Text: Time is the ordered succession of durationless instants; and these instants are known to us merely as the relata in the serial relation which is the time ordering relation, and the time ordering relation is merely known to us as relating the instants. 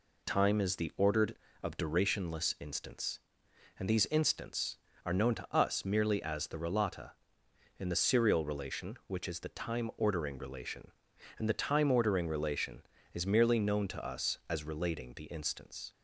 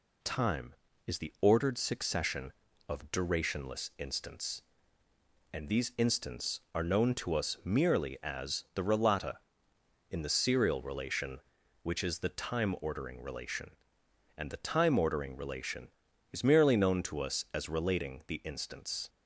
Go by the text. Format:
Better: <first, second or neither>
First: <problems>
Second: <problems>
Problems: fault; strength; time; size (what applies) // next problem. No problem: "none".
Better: second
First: skips "succession"; at 1.4 s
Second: none